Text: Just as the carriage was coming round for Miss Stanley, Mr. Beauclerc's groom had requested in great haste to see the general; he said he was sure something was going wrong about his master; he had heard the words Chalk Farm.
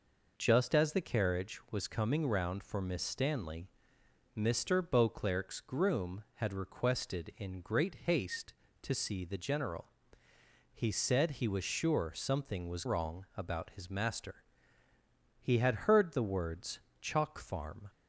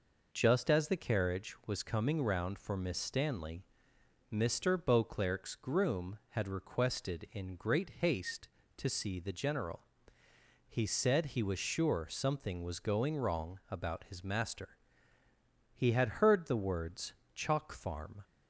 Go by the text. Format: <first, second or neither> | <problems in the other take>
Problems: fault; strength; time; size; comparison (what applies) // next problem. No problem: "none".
second | skips "going"; at 12.8 s // pauses between "words" and "Chalk"; slight; at 16.7 s; 0.22 s long; slight in the second